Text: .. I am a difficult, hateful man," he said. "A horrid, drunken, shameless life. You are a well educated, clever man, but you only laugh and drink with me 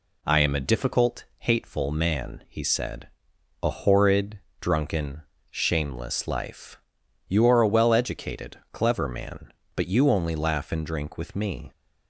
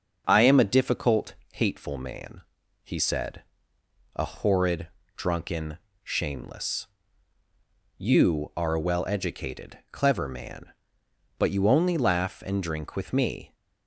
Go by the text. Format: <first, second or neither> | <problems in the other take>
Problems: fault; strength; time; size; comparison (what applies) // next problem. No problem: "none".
first | starts louder than the rest; until 1.2 s; 6.5 dB // skips "life"; at 7.4 s